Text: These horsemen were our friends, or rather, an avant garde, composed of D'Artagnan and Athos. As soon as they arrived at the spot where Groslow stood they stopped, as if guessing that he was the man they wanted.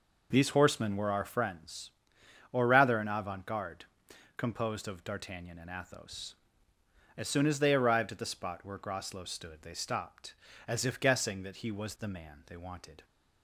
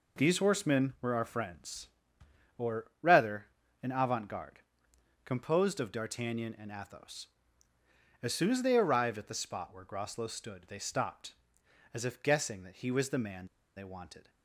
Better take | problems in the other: first | pauses between "or" and "rather"; slight; at 2.8 s; 0.16 s long // pauses between "man" and "they"; slight; at 13.4 s; 0.31 s long

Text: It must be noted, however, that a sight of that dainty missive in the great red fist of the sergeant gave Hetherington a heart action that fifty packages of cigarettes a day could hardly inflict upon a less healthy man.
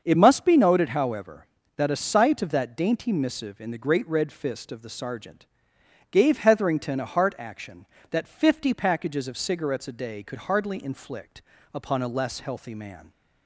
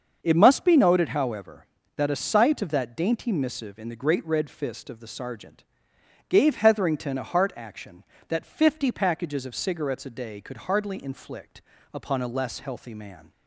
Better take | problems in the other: neither | starts louder than the rest; the same in both // pauses between "sergeant" and "gave"; noticeable; the same in both // pauses between "inflict" and "upon"; slight; the same in both

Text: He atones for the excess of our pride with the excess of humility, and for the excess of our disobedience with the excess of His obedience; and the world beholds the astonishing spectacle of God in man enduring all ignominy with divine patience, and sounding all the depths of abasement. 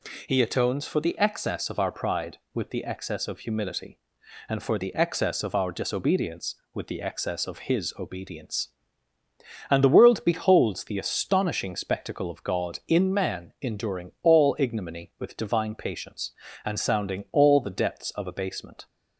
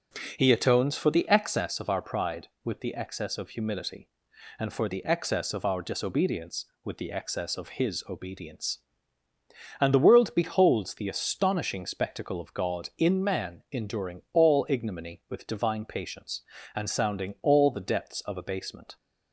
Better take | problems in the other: first | starts louder than the rest; noticeable; until 1.7 s; 5 dB

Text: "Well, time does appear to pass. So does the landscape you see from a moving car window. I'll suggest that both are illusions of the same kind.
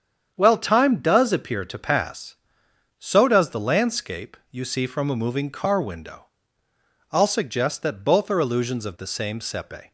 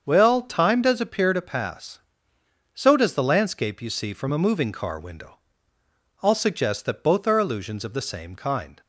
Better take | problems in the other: second | starts louder than the rest; strong; until 1.3 s; 8 dB; also in the second // says "sepe" for "kind"; at 9.4 s

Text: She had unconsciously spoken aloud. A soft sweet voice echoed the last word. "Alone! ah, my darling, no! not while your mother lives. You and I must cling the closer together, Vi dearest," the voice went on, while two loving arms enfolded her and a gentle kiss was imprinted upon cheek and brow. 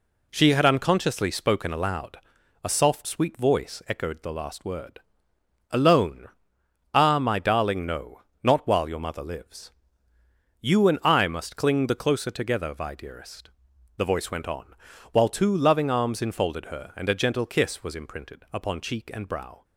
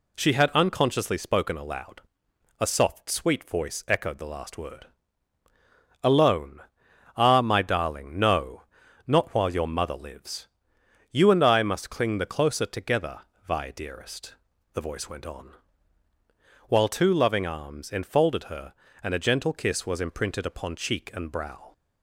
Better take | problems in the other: neither | none

